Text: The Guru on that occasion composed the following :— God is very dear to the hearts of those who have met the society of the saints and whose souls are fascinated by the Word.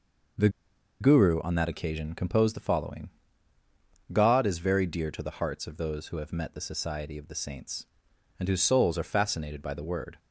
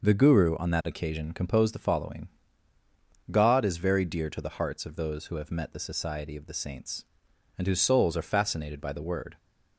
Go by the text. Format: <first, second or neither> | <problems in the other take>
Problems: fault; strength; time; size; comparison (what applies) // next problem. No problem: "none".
second | pauses between "The" and "Guru"; noticeable; at 0.4 s; 0.51 s long